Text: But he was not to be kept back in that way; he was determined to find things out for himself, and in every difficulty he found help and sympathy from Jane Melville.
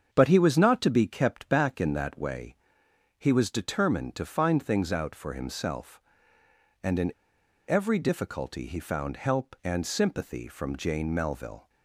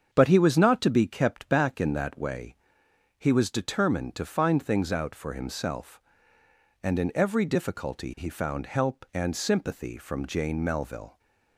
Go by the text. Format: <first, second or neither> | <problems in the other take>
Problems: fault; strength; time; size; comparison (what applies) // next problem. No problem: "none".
second | starts louder than the rest; strong; until 1.1 s; 7 dB; strong in the second // pauses between "in" and "every"; noticeable; at 7.1 s; 0.55 s long